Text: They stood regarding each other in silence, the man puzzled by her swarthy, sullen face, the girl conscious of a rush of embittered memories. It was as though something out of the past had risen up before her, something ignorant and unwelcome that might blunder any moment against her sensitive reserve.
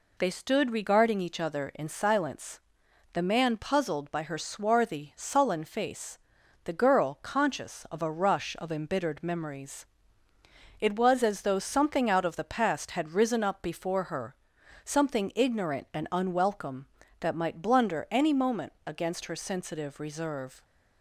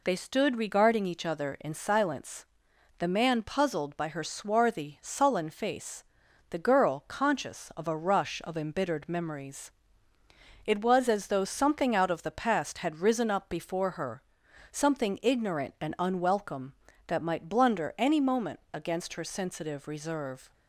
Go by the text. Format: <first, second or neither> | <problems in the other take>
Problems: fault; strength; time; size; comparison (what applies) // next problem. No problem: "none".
neither | none